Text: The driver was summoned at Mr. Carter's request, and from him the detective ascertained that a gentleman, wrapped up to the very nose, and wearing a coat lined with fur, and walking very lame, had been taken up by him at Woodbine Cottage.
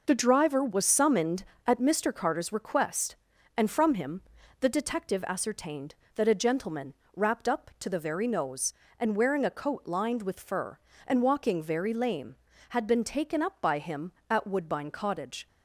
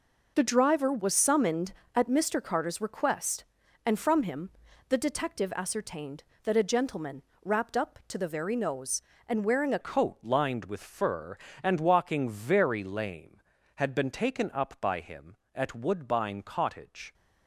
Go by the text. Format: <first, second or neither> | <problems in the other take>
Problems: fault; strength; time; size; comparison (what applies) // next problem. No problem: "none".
first | pauses between "him" and "the"; at 4.5 s; 0.38 s long; also in the first // changes voice at "coat"; from 9.8 s on; 7.3 s long